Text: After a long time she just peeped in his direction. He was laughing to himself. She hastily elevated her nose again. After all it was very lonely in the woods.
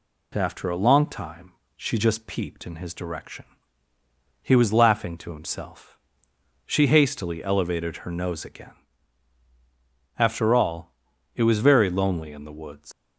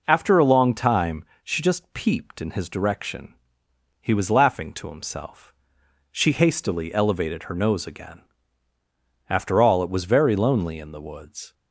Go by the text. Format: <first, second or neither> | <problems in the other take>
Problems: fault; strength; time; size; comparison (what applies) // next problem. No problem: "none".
second | pauses between "time" and "she"; slight; at 1.5 s; 0.26 s long; slight in the second // pauses between "all" and "it"; at 10.9 s; 0.44 s long // leaves "woods" unfinished; at 12.9 s; 135 ms